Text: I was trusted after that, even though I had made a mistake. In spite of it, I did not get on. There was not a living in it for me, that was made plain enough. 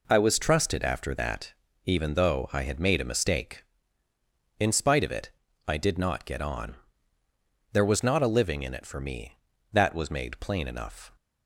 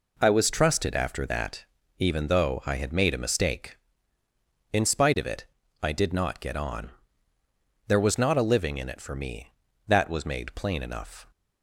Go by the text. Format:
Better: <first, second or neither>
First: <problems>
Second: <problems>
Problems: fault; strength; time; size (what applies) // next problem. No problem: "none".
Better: neither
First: none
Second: none